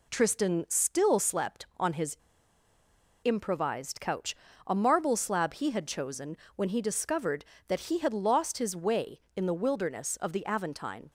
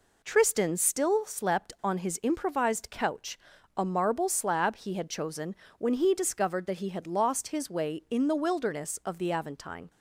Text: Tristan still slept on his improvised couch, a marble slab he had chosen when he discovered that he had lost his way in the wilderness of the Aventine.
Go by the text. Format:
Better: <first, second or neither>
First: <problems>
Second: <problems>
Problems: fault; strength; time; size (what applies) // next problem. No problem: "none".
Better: second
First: pauses between "his" and "improvised"; at 2.1 s; 1.0 s long // pauses between "chosen" and "when"; slight; at 6.3 s; 0.20 s long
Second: pauses between "chosen" and "when"; slight; at 5.5 s; 0.24 s long